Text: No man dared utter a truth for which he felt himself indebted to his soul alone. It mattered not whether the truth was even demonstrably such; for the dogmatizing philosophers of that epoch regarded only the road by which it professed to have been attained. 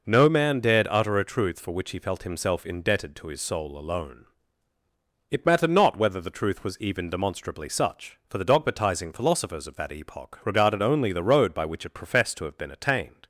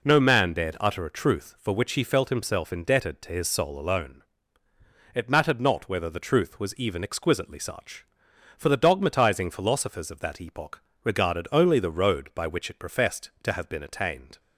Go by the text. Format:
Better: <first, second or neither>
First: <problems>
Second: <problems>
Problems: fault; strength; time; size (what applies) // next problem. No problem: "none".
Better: first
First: none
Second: says "exquisitely" for "demonstrably"; at 7.0 s // pauses between "epoch" and "regarded"; slight; at 10.8 s; 0.22 s long